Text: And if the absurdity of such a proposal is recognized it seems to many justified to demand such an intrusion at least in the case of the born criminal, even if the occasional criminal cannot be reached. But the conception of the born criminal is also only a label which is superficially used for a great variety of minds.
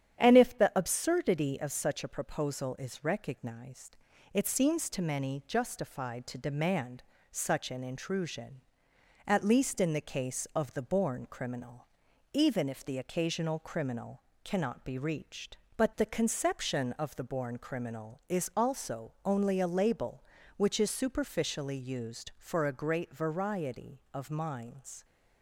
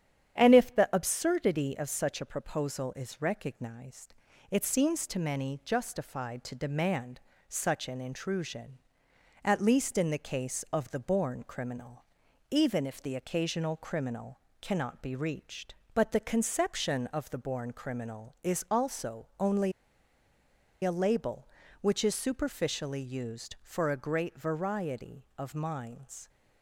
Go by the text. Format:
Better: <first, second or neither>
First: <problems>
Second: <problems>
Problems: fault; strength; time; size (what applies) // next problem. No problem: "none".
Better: first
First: starts louder than the rest; strong; until 1.2 s; 9.5 dB // pauses between "recognized" and "it"; slight; at 3.9 s; 0.36 s long // pauses between "demand" and "such"; slight; at 7.0 s; 0.30 s long // pauses between "criminal" and "cannot"; slight; at 14.2 s; 0.22 s long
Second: starts louder than the rest; strong; until 1.4 s; 9.5 dB // pauses between "recognized" and "it"; slight; at 4.1 s; 0.36 s long // pauses between "demand" and "such"; slight; at 7.1 s; 0.30 s long // pauses between "criminal" and "cannot"; slight; at 14.3 s; 0.22 s long // pauses between "only" and "a"; at 19.7 s; 1.1 s long